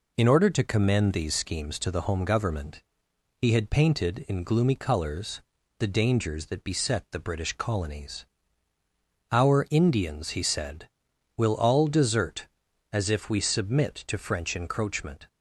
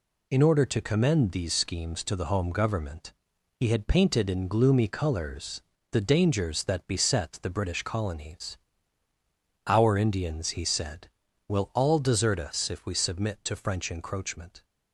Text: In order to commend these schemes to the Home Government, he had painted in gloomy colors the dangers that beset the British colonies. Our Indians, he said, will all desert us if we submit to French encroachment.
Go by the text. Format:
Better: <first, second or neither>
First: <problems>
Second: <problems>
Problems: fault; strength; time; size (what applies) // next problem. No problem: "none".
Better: second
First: pauses between "colors" and "the"; at 5.4 s; 0.38 s long // says "as" for "us"; at 12.9 s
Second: pauses between "colors" and "the"; slight; at 5.6 s; 0.30 s long